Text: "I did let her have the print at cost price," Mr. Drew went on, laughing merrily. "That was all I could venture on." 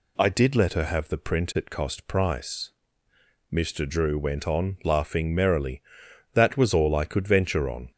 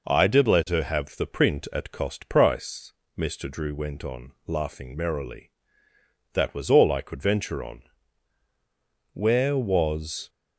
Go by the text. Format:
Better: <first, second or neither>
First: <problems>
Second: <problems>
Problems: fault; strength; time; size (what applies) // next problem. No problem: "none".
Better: first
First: none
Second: goes on to say "Where was"; noticeable; from 9.1 s on; 1.1 s long